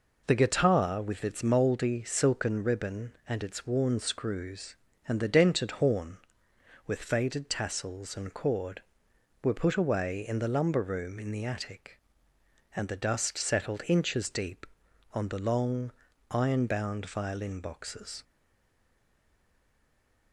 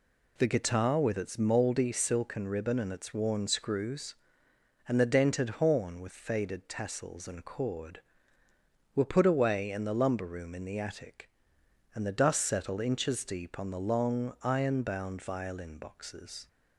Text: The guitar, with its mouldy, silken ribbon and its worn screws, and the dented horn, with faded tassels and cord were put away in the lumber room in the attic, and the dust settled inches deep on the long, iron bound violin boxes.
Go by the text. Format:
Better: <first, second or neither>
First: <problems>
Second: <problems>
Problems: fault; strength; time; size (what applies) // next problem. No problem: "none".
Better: second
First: stays silent after the last word; noticeable; from 18.2 s on; 2.1 s long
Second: none